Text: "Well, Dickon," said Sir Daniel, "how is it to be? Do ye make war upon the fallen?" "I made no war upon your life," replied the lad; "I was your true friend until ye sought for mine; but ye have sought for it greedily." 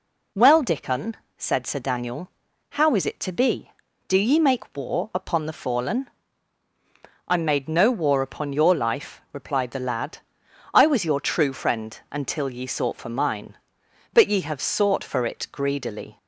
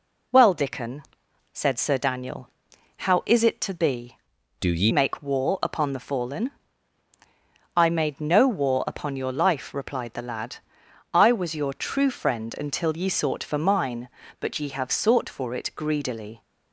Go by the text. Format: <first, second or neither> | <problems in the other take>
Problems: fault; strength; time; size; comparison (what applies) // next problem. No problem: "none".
first | changes voice from "Do" to "ye"; from 4.5 to 4.9 s; 0.4 s long